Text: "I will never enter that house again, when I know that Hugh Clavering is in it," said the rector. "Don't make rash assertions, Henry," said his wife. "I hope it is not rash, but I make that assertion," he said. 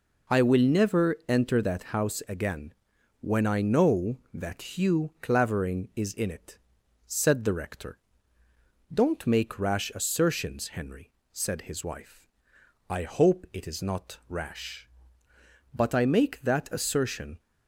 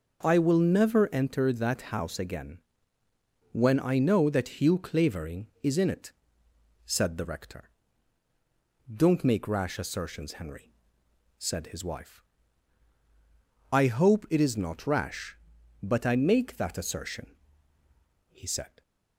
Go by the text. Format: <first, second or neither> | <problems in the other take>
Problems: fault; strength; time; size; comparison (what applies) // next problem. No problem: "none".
second | stops before "he said"; at 17.3 s